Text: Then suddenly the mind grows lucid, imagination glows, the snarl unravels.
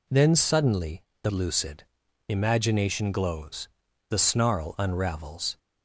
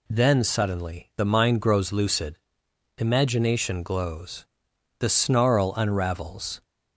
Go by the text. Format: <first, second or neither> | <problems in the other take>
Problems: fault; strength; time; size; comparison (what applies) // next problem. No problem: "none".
second | pauses between "suddenly" and "the"; slight; at 1.0 s; 0.18 s long // skips "mind grows"; at 1.3 s